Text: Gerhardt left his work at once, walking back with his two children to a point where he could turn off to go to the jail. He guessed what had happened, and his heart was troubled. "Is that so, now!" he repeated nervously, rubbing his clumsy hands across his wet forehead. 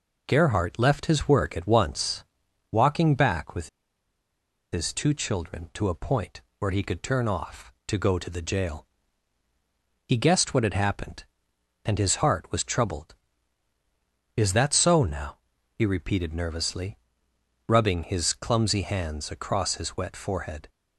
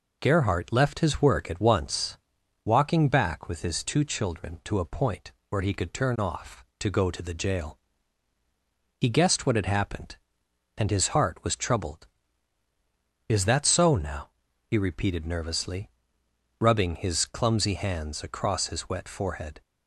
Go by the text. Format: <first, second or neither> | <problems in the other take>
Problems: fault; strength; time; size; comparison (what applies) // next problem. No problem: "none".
second | pauses between "with" and "his"; at 3.6 s; 1.0 s long // pauses between "point" and "where"; slight; at 6.4 s; 0.18 s long; slight in the second